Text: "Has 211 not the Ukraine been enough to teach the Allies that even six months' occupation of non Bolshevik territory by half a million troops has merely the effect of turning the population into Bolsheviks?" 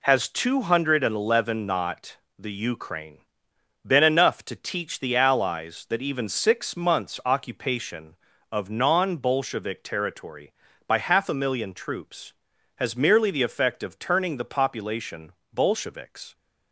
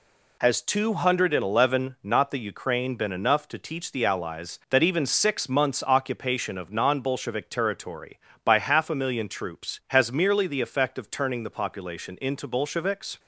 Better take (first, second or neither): second